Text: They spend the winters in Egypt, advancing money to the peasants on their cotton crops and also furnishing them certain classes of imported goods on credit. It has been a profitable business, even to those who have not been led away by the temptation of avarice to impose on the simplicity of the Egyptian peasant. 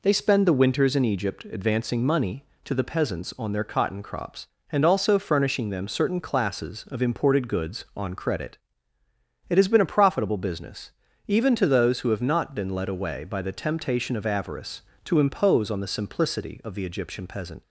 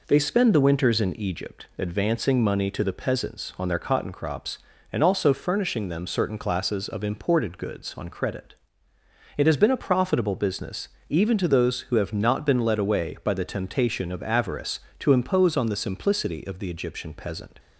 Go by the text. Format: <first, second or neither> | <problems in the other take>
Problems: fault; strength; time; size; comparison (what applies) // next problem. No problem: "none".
neither | none